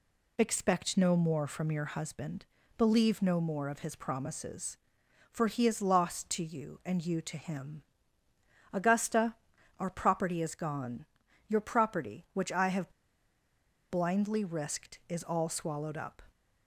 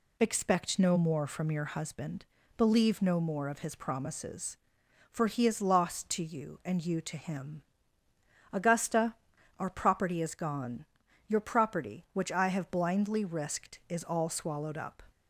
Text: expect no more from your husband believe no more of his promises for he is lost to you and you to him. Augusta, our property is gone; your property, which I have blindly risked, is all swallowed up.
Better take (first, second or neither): second